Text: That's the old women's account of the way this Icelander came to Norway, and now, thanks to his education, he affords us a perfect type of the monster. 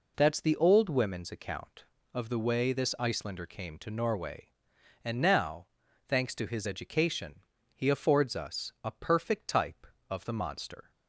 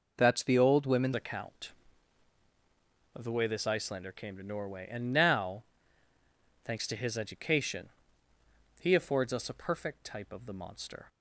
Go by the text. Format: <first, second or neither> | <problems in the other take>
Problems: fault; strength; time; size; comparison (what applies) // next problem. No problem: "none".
first | changes voice at "account"; from 1.1 s on; 9.9 s long